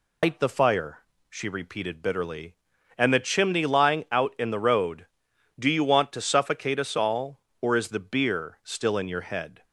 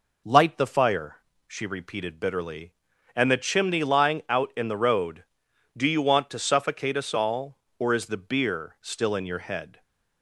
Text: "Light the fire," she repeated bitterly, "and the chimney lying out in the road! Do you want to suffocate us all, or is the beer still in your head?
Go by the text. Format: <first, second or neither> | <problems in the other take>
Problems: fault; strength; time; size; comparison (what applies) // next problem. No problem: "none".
second | loses the start of "Light"; at 0.2 s; 150 ms